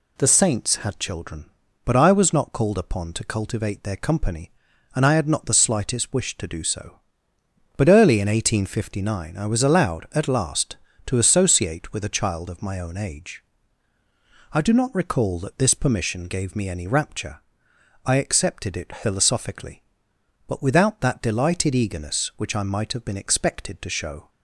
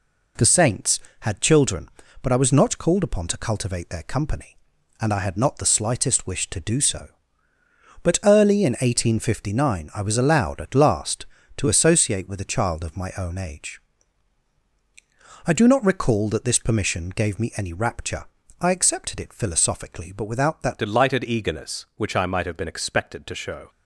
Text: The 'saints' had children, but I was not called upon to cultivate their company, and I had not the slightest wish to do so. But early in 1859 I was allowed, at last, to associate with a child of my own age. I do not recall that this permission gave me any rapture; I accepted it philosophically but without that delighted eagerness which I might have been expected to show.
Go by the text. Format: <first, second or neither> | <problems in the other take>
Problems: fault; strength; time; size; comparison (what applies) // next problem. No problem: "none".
first | changes voice at "delighted"; from 20.7 s on; 2.9 s long